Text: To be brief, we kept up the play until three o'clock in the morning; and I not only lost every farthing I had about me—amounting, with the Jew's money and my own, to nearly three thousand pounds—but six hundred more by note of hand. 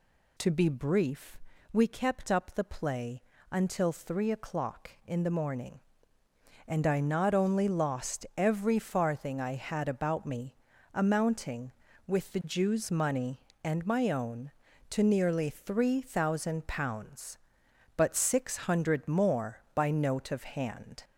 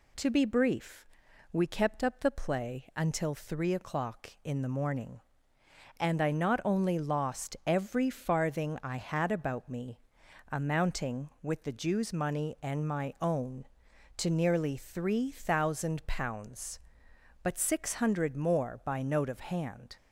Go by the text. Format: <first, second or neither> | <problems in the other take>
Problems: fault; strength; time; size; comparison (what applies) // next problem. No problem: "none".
second | gets louder; slight; throughout; 2 dB // pauses between "play" and "until"; slight; at 3.2 s; 0.28 s long